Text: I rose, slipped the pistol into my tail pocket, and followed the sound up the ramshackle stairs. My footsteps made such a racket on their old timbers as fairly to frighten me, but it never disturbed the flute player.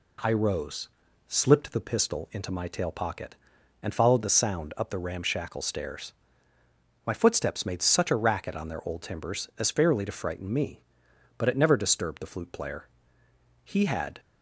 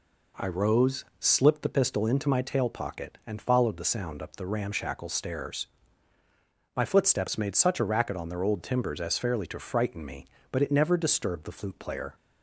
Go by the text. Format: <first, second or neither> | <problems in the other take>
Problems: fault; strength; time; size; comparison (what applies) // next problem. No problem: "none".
second | goes on to say "He had"; from 13.6 s on; 0.56 s long